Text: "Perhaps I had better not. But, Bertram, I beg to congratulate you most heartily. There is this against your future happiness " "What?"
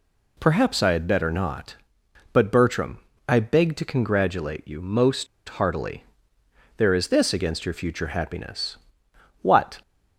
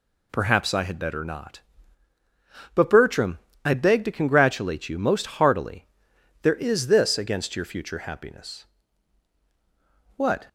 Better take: second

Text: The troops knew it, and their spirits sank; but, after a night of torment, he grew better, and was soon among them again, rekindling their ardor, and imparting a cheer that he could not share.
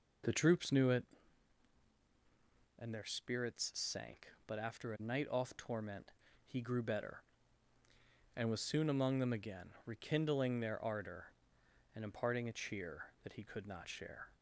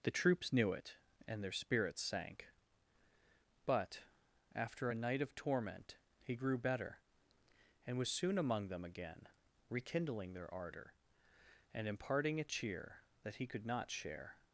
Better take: second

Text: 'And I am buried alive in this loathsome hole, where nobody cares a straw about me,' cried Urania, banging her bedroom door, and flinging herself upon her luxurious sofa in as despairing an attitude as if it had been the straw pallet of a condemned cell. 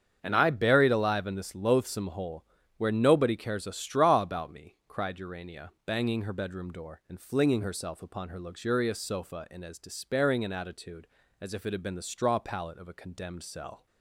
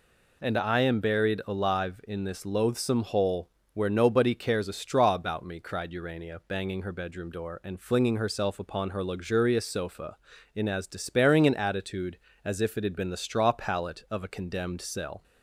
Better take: second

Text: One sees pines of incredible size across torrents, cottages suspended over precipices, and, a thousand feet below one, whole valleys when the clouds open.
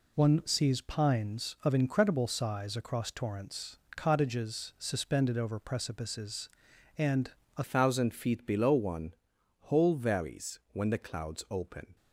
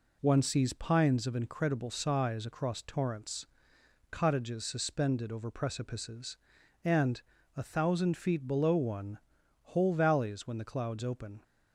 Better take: second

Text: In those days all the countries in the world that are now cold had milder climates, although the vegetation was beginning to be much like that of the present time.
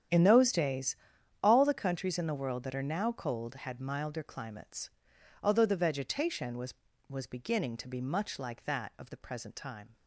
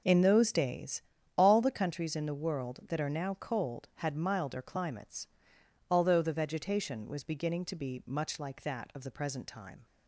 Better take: second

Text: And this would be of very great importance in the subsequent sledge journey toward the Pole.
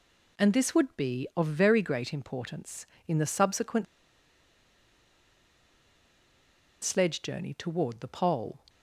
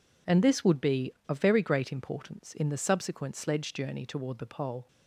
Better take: second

